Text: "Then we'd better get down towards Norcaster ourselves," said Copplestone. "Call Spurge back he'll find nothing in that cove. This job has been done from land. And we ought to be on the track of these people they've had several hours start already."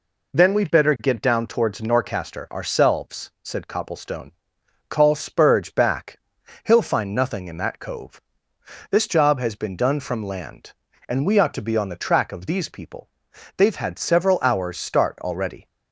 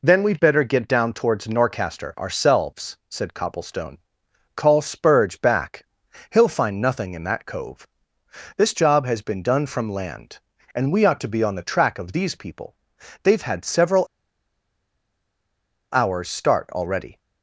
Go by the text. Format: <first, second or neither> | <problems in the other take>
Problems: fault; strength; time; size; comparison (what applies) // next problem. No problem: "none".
first | pauses between "back" and "he'll"; noticeable; at 5.8 s; 0.46 s long; noticeable in the first // pauses between "people" and "they've"; noticeable; at 12.7 s; 0.48 s long; noticeable in the first // pauses between "several" and "hours"; strong; at 14.0 s; 1.8 s long